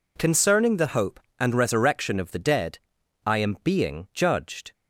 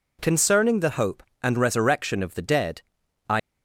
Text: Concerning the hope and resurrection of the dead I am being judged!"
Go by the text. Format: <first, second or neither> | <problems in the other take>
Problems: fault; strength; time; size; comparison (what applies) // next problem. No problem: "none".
first | pauses between "dead" and "I"; noticeable; at 2.8 s; 0.48 s long; noticeable in the first // stops before "am being judged"; at 3.3 s